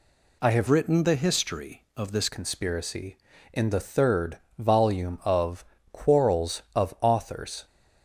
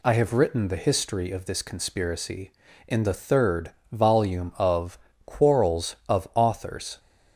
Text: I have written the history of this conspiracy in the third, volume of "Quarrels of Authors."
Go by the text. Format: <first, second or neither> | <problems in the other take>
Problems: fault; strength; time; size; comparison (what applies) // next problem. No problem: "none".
second | changes voice from "written" to "this"; from 0.6 to 2.2 s; 1.6 s long // pauses between "of" and "Quarrels"; slight; at 5.6 s; 0.26 s long; slight in the second